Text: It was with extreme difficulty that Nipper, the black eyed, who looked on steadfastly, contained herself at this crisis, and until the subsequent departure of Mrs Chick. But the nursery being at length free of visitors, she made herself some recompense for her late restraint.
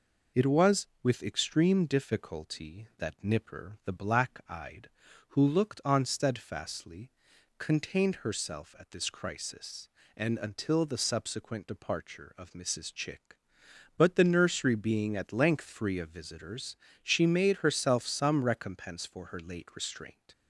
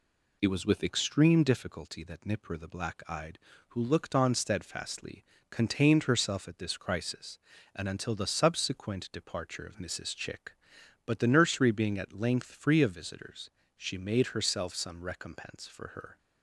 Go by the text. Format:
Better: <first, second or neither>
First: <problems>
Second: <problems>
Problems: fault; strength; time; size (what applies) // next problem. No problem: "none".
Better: first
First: none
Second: stops before "late restraint"; at 16.1 s